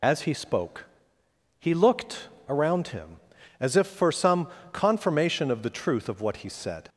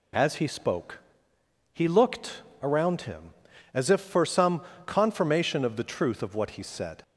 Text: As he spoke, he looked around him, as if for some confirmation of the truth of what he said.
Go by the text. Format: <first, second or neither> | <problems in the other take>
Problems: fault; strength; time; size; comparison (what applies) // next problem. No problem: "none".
second | loses the start of "As"; at 0.0 s; 35 ms // pauses between "looked" and "around"; slight; at 2.2 s; 0.20 s long; slight in the second // pauses between "some" and "confirmation"; slight; at 4.4 s; 0.26 s long; slight in the second